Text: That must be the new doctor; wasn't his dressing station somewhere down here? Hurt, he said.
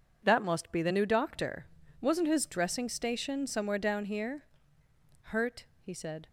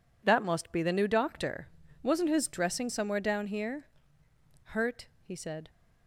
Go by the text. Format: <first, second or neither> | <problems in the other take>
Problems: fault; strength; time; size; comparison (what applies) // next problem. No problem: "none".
first | skips "station"; at 2.8 s